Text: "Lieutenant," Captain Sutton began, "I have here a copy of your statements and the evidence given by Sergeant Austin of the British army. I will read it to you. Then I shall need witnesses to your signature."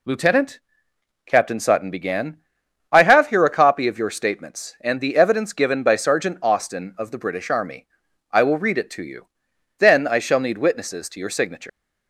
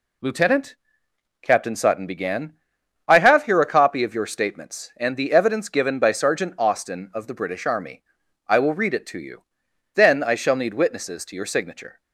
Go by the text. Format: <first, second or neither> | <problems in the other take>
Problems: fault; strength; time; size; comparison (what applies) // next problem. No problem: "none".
second | leaves "signature" unfinished; at 11.6 s; 150 ms